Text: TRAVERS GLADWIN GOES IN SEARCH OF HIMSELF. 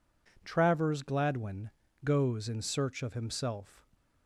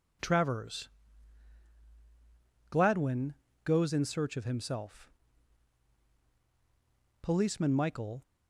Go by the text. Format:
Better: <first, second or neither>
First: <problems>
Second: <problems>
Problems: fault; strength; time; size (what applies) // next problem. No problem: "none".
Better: first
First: pauses between "GLADWIN" and "GOES"; slight; at 1.6 s; 0.34 s long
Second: pauses between "TRAVERS" and "GLADWIN"; strong; at 0.9 s; 1.7 s long // pauses between "GLADWIN" and "GOES"; slight; at 3.3 s; 0.32 s long // goes on to say "Policeman Michael"; noticeable; from 7.2 s on; 1.0 s long